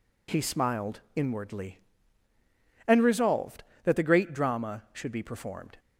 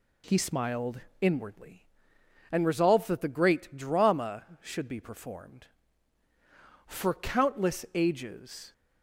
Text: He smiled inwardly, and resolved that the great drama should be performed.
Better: first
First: pauses between "smiled" and "inwardly"; slight; at 0.9 s; 0.16 s long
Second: pauses between "smiled" and "inwardly"; slight; at 1.0 s; 0.20 s long // goes on to say "For countless ages"; strong; from 6.8 s on; 1.8 s long

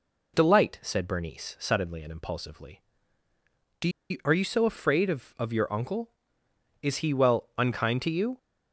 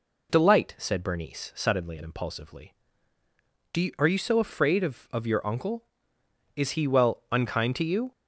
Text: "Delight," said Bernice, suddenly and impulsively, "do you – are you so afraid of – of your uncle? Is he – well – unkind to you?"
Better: second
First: pauses between "do" and "you"; slight; at 3.8 s; 0.21 s long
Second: none

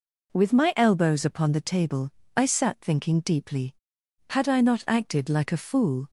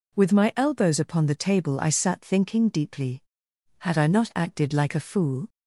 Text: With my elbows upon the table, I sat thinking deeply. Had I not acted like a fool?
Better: neither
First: none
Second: none

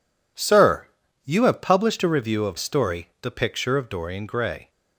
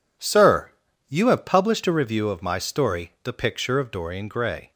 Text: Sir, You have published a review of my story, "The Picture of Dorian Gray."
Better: second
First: skips "my"; at 2.5 s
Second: none

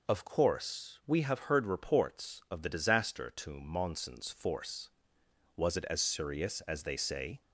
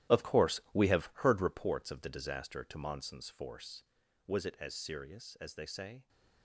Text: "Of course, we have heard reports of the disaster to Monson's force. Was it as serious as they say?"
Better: first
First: none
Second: gets quieter; strong; throughout; 13.5 dB

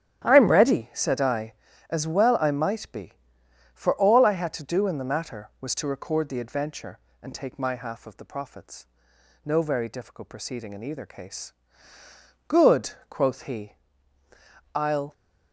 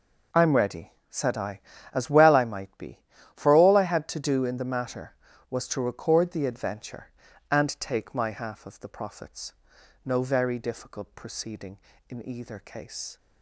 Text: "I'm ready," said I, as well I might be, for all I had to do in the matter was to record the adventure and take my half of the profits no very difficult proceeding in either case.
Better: second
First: starts louder than the rest; strong; until 1.2 s; 11.5 dB // pauses between "profits" and "no"; noticeable; at 8.8 s; 0.58 s long // goes on to say "Good quoth he I'll"; strong; from 12.4 s on; 2.6 s long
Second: pauses between "profits" and "no"; noticeable; at 9.5 s; 0.54 s long

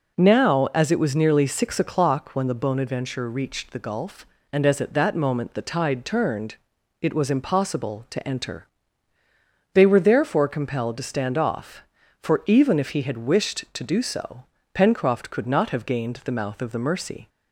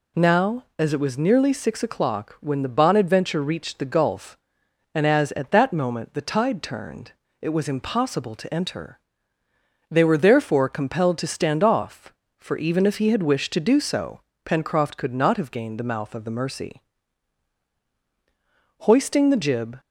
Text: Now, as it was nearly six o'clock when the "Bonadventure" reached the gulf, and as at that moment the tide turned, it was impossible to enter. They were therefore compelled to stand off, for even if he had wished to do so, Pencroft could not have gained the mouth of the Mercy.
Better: first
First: none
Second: goes on to say "Hoisting the jib"; noticeable; from 18.7 s on; 1.0 s long

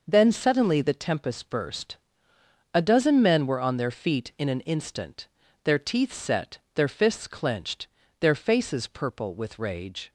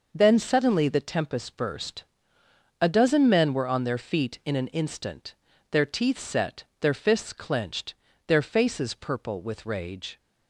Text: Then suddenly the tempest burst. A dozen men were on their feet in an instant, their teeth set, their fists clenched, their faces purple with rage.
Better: neither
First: none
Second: none

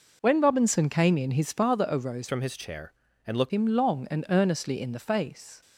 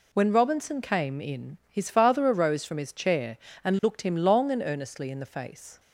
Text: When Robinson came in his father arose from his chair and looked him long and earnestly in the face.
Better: second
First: changes voice from "from" to "looked"; from 2.2 to 3.5 s; 1.3 s long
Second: none

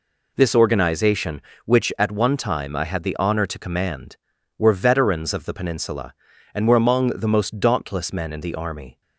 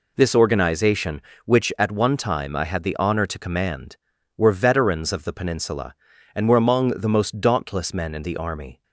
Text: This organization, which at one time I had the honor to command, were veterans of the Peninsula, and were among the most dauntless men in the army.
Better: neither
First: none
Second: none

